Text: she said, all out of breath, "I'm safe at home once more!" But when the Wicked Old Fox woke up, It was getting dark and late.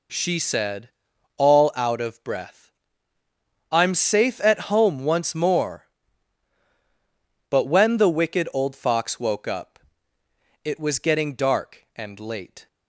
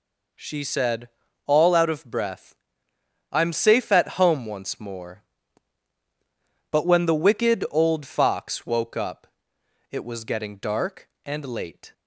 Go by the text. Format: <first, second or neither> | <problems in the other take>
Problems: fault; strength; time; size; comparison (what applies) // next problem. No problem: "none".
neither | none